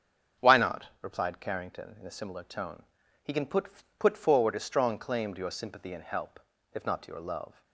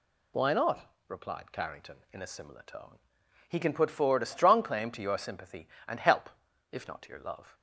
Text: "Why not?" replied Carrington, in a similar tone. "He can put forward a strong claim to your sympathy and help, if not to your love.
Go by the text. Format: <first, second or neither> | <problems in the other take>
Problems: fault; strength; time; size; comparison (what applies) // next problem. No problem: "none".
second | starts louder than the rest; strong; until 1.5 s; 7.5 dB // says "put" twice; at 3.9 s